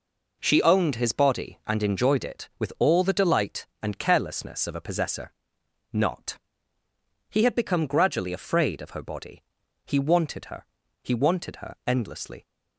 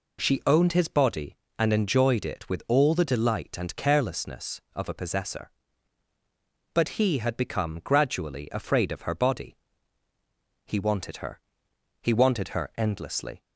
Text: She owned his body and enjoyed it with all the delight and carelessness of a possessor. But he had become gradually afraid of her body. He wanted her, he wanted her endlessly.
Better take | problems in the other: second | says "Not" for "But"; at 5.9 s

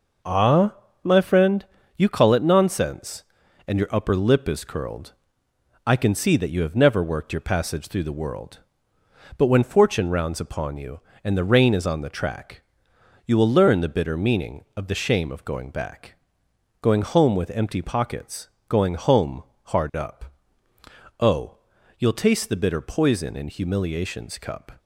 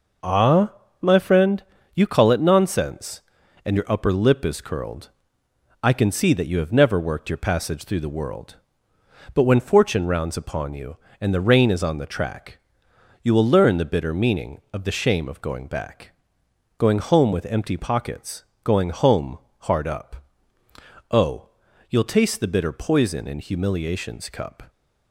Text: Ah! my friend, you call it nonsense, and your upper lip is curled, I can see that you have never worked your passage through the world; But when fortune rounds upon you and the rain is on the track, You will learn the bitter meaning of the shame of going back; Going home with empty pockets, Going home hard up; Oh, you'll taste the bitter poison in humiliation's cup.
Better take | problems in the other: neither | pauses between "home" and "hard"; slight; the same in both

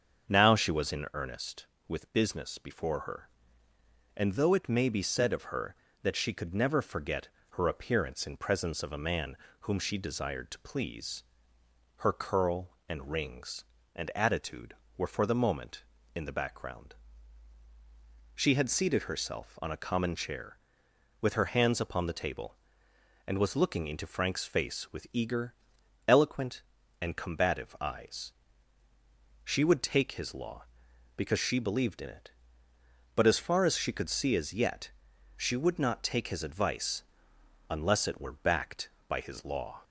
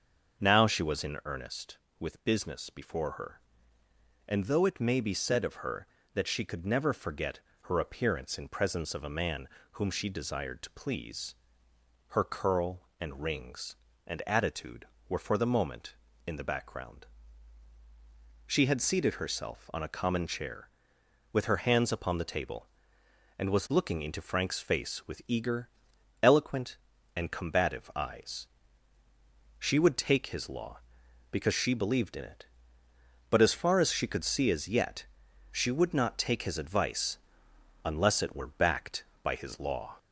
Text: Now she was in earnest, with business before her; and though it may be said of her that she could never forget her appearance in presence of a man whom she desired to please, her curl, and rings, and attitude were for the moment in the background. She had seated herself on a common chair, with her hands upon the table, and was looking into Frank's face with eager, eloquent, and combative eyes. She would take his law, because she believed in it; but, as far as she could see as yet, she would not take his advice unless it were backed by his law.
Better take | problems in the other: first | gets louder; slight; throughout; 2.5 dB // starts louder than the rest; until 1.4 s; 6.5 dB; also in the first // pauses between "forget" and "her"; slight; at 7.3 s; 0.22 s long; slight in the first // pauses between "man" and "whom"; slight; at 9.4 s; 0.26 s long; slight in the first // pauses between "advice" and "unless"; noticeable; at 37.1 s; 0.66 s long; noticeable in the first

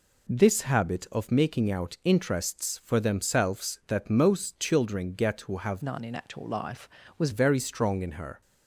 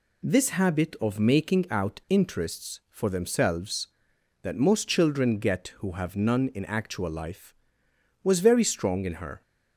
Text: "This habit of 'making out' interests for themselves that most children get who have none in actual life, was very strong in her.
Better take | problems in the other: second | changes voice from "none" to "was"; from 5.8 to 7.2 s; 1.4 s long

